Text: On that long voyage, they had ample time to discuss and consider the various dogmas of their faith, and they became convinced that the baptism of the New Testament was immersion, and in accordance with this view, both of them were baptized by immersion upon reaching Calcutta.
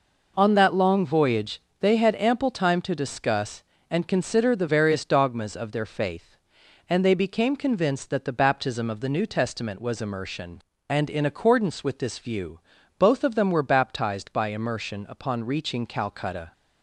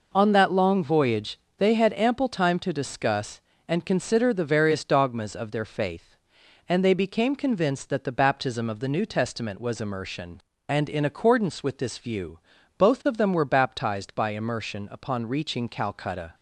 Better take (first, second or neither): neither